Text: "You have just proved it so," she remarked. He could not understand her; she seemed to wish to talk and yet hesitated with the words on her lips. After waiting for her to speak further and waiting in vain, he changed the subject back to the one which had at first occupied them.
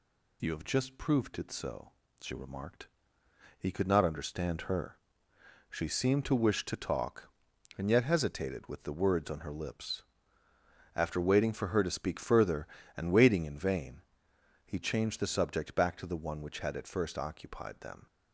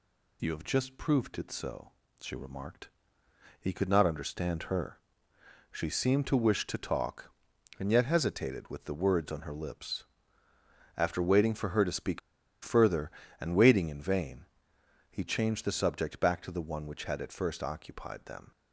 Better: first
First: none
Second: pauses between "speak" and "further"; at 12.1 s; 0.45 s long

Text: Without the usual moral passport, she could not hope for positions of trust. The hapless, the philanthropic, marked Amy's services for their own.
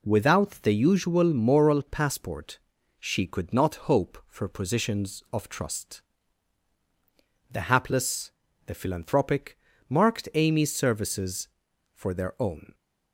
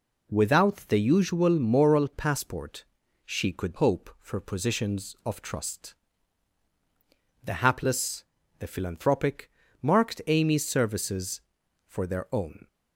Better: first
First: none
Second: skips "not"; at 3.7 s

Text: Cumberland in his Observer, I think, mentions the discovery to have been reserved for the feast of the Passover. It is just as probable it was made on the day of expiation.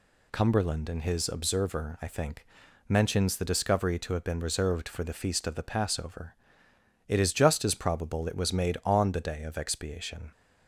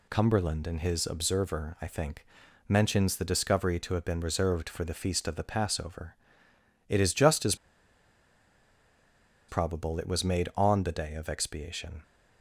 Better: first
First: none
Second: pauses between "as" and "probable"; strong; at 7.5 s; 1.9 s long

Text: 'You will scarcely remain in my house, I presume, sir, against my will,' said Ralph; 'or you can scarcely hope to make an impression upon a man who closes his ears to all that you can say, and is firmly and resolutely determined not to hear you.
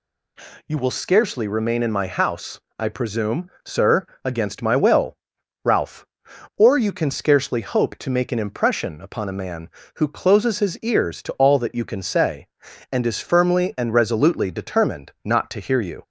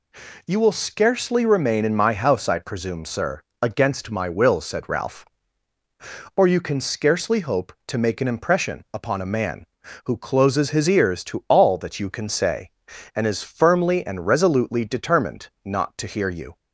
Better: second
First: skips "said"; at 5.3 s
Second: none

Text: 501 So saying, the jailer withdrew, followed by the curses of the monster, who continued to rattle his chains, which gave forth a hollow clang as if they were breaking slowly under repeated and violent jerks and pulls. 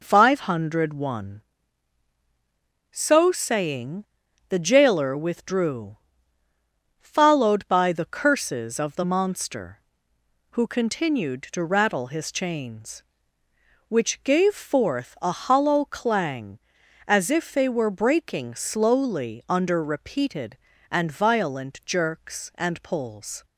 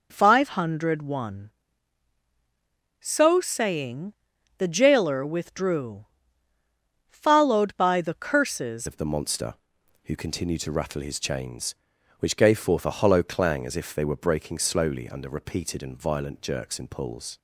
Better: first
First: none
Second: changes voice at "of"; from 8.8 s on; 8.5 s long

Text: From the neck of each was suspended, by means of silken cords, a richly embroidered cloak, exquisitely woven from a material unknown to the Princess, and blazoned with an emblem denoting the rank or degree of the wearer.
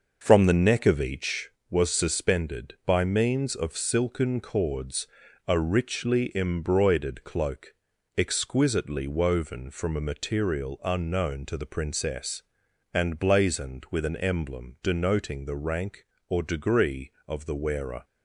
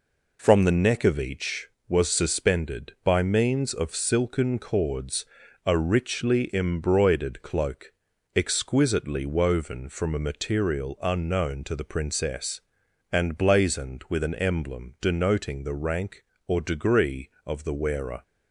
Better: second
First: starts louder than the rest; noticeable; until 1.6 s; 6 dB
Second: none

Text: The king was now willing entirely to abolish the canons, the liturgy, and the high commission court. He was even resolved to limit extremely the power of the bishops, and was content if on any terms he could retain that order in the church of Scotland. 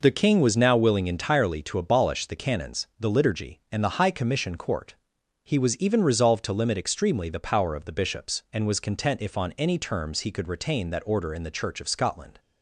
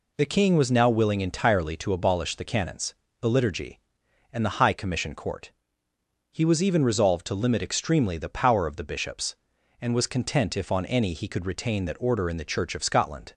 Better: first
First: none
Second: skips "terms"; at 11.1 s

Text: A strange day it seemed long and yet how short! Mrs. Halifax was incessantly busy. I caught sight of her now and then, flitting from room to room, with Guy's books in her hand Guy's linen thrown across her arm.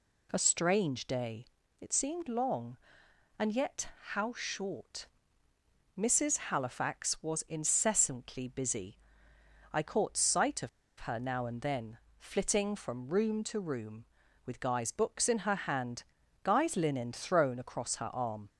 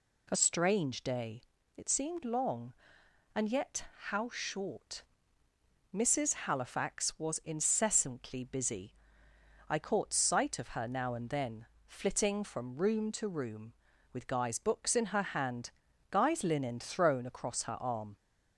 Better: second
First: pauses between "day" and "it"; slight; at 1.4 s; 0.36 s long // pauses between "yet" and "how"; slight; at 3.8 s; 0.24 s long // pauses between "of" and "her"; slight; at 10.6 s; 0.31 s long // pauses between "hand" and "Guy's"; at 16.0 s; 0.40 s long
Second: pauses between "day" and "it"; slight; at 1.4 s; 0.36 s long // pauses between "yet" and "how"; slight; at 3.8 s; 0.24 s long // pauses between "hand" and "Guy's"; at 15.6 s; 0.40 s long

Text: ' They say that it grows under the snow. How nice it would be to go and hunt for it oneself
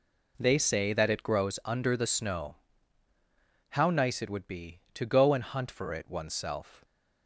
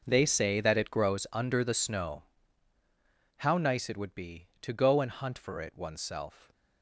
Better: first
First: none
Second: gets quieter; strong; throughout; 15 dB

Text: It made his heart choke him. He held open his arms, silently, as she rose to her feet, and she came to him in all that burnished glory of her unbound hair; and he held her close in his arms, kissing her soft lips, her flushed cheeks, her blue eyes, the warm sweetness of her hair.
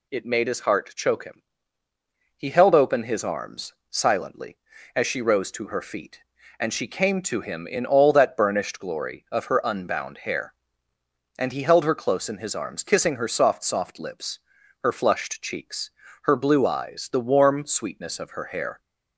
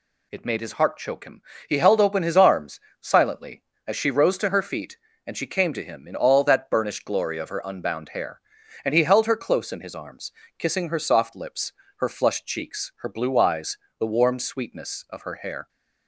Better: second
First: says "soft" twice; at 13.6 s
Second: none

